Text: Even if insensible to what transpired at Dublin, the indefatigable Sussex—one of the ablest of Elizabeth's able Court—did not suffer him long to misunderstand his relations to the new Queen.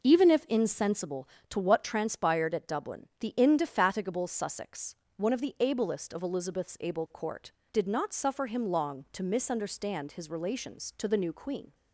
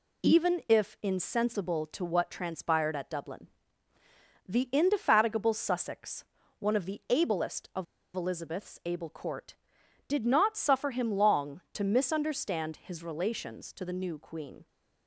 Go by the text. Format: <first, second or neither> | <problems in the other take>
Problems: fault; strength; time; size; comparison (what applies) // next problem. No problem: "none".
first | pauses between "of" and "Elizabeth's"; slight; at 7.8 s; 0.29 s long